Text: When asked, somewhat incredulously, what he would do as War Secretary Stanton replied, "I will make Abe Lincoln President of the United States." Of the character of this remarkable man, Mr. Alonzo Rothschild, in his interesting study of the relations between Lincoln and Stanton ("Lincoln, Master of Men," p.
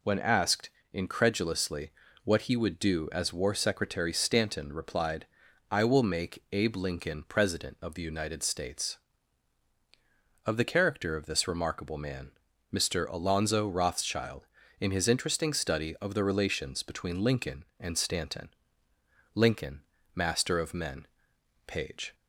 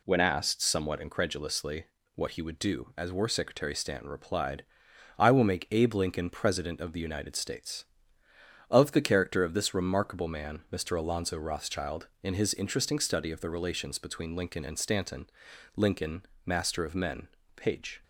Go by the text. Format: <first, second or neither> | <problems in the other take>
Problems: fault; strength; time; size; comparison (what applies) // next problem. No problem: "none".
second | skips "somewhat"; at 0.8 s